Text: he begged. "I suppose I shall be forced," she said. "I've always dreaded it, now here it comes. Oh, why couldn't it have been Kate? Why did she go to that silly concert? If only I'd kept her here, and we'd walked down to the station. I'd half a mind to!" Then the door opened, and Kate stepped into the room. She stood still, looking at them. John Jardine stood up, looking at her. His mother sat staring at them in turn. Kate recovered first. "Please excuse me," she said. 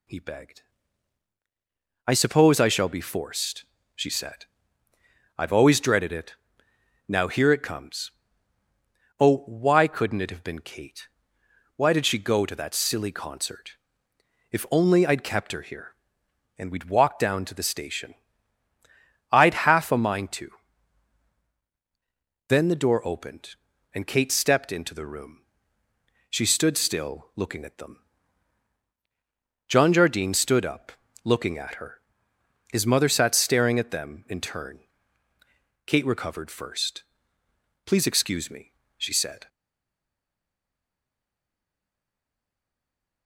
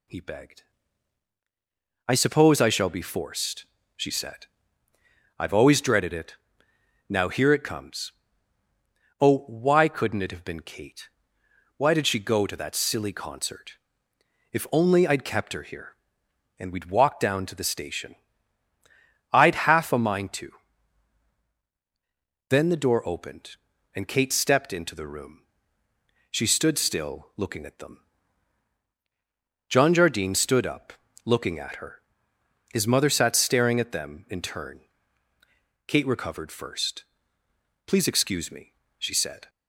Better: second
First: stays silent after the last word; strong; from 39.4 s on; 3.8 s long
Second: none

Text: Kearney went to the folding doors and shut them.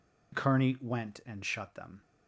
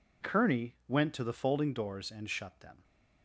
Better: second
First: skips "to the folding doors"; at 1.2 s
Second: none

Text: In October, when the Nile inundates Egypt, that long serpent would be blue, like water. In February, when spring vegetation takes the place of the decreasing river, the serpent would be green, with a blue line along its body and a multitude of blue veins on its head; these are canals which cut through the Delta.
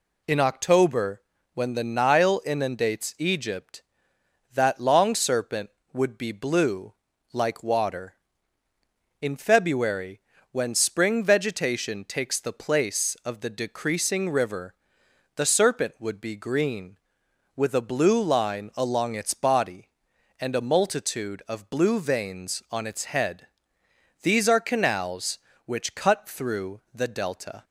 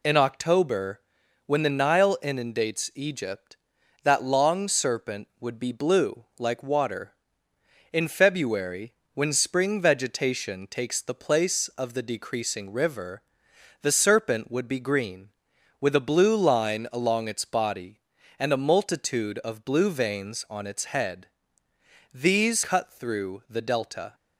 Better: first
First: none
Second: skips "are canals which"; at 22.6 s

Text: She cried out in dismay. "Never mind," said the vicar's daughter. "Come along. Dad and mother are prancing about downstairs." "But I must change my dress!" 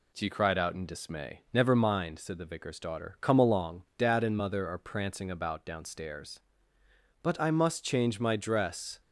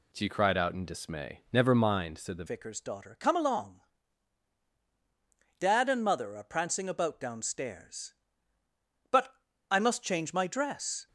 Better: first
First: none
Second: changes voice at "vicar's"; from 2.4 s on; 8.6 s long // pauses between "But" and "I"; slight; at 9.3 s; 0.36 s long

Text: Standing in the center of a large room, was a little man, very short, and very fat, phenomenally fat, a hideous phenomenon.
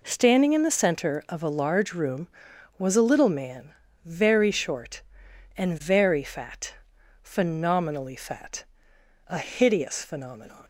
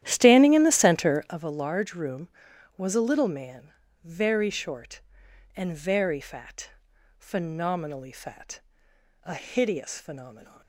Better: first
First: none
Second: starts louder than the rest; strong; until 1.4 s; 12 dB

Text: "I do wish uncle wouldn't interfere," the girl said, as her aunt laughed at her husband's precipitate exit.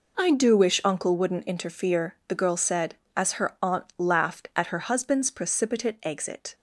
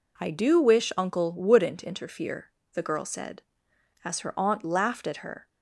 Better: first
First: none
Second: stops before "husband's precipitate exit"; at 5.4 s

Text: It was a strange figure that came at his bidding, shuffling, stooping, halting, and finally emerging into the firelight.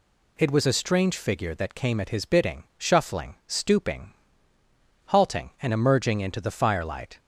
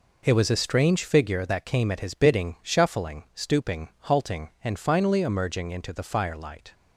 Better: second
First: skips "finally"; at 5.7 s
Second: none

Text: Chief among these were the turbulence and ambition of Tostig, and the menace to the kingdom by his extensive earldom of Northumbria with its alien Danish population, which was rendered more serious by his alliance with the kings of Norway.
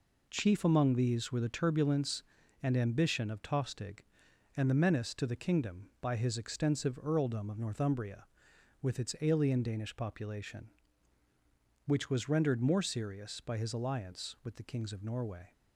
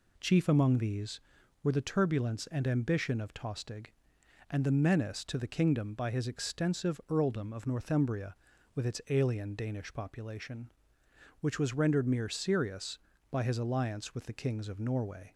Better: first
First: none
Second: says "mere" for "more"; at 12.0 s

